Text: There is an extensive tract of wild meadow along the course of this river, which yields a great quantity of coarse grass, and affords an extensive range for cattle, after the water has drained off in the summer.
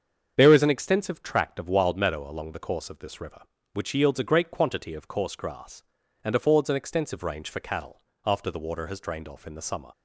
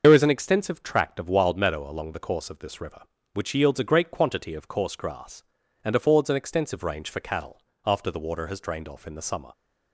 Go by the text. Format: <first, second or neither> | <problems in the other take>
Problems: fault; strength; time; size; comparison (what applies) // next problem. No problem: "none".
first | loses the start of "There"; at 0.0 s; 70 ms // starts louder than the rest; until 1.0 s; 6.5 dB; strong in the first